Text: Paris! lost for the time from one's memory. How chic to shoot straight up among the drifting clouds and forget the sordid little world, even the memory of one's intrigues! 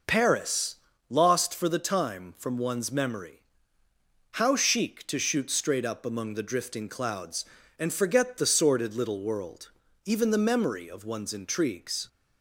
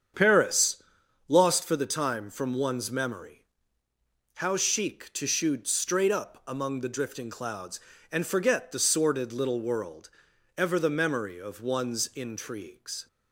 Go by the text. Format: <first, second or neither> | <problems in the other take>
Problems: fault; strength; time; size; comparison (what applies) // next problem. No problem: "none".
first | starts louder than the rest; strong; until 1.6 s; 7.5 dB // says "ever" for "even"; at 10.5 s